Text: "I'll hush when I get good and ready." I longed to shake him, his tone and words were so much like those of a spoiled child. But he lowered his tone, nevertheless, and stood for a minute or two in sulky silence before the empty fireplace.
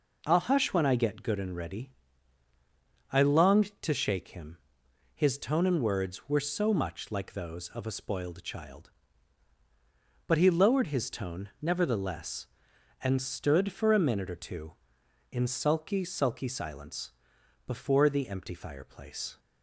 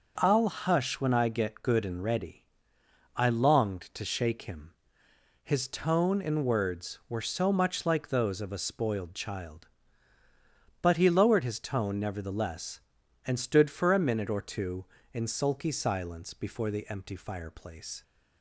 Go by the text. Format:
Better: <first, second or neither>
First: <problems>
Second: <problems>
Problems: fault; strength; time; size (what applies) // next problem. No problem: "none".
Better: second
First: says "sulky" twice; at 16.0 s // pauses between "silence" and "before"; noticeable; at 17.1 s; 0.54 s long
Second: none